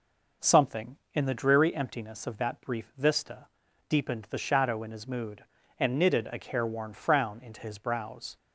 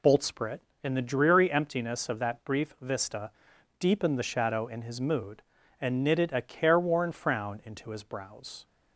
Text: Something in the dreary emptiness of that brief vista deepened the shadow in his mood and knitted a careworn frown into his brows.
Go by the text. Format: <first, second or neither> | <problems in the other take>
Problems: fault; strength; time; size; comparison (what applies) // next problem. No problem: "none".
first | says "Boltsprit" for "Something"; at 0.0 s // pauses between "vista" and "deepened"; noticeable; at 3.3 s; 0.48 s long; also in the first